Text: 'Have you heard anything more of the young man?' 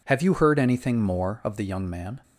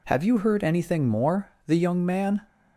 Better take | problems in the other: first | skips "of"; at 1.5 s

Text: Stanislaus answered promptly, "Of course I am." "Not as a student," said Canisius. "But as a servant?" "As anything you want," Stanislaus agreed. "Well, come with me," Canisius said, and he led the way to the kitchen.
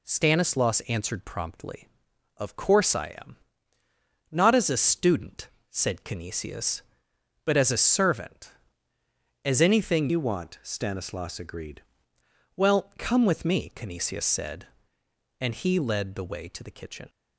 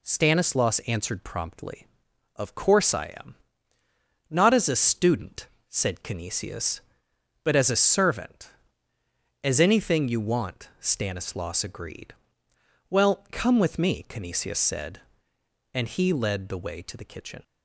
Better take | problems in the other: second | changes voice from "you" to "agreed"; from 10.0 to 11.8 s; 1.8 s long

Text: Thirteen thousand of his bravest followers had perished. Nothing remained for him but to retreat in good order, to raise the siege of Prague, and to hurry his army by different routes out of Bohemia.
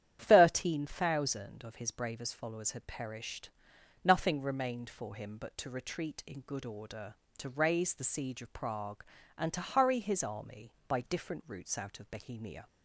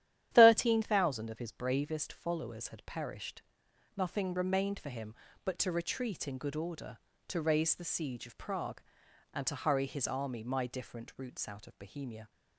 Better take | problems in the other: first | starts louder than the rest; strong; until 1.3 s; 11 dB; strong in the first // says "my" for "by"; at 10.4 s

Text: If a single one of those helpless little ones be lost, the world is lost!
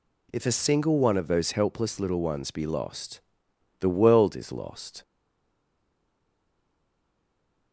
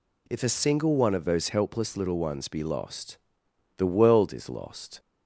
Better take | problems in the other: second | stays silent after the last word; strong; from 5.0 s on; 2.7 s long

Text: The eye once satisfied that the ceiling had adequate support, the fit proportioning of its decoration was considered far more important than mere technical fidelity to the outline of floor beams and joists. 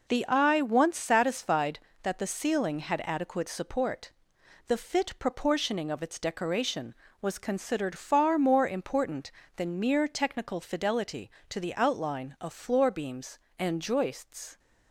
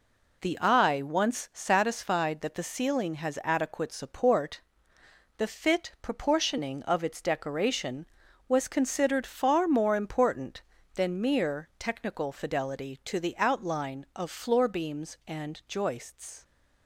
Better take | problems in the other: first | says "has" for "had"; at 3.1 s

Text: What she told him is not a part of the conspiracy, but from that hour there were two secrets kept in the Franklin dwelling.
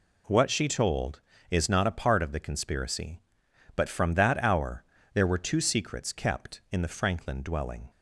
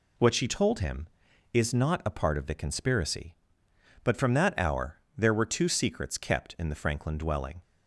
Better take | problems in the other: second | skips "him"; at 1.3 s // pauses between "hour" and "there"; slight; at 4.8 s; 0.30 s long; slight in the second

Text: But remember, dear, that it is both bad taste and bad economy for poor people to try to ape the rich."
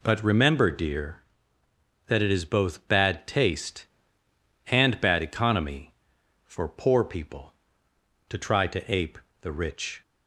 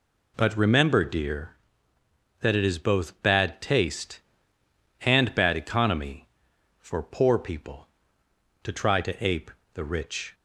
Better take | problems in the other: neither | pauses between "ape" and "the"; slight; the same in both

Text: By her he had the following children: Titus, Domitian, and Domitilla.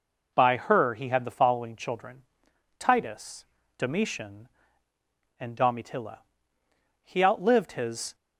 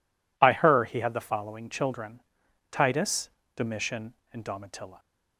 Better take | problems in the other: second | goes on to say "He outlived his"; noticeable; from 7.0 s on; 1.1 s long

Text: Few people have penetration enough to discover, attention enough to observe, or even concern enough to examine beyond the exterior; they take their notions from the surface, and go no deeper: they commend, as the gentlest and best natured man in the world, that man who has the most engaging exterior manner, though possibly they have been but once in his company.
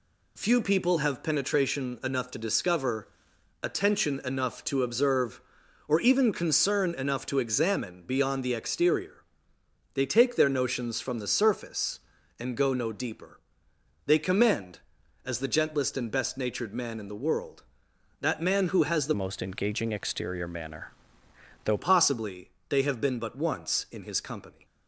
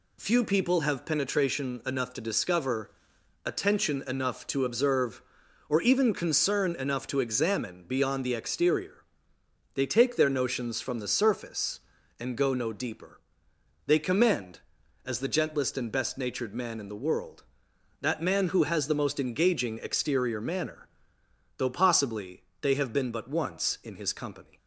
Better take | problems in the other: second | changes voice from "most" to "though"; from 19.1 to 21.7 s; 2.6 s long // pauses between "possibly" and "they"; slight; at 22.4 s; 0.22 s long; slight in the second

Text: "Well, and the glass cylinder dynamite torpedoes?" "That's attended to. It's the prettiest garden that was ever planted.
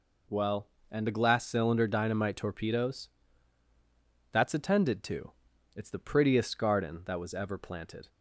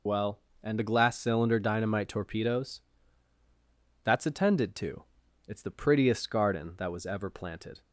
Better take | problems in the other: first | loses the start of "Well"; at 0.0 s; 50 ms

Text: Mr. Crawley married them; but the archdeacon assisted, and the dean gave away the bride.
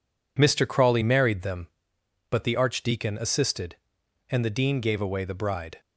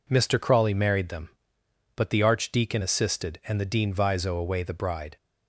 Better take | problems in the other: first | says "viso" for "gave"; at 3.9 s

